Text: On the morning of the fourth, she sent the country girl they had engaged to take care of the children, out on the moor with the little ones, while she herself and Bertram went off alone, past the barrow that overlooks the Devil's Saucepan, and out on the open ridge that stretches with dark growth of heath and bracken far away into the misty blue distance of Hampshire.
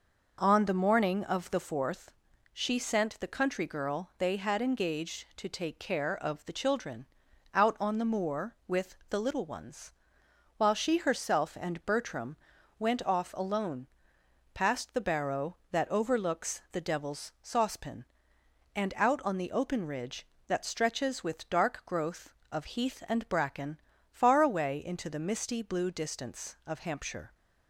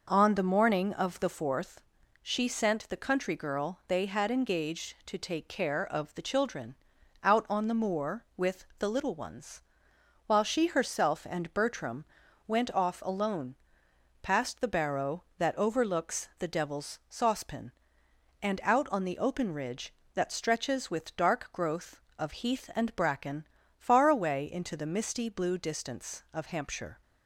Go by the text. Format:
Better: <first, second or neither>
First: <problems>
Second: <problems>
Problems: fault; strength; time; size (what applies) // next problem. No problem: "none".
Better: neither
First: pauses between "Bertram" and "went"; at 12.3 s; 0.42 s long // pauses between "bracken" and "far"; slight; at 23.7 s; 0.32 s long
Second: pauses between "Bertram" and "went"; at 12.0 s; 0.42 s long // pauses between "bracken" and "far"; slight; at 23.4 s; 0.32 s long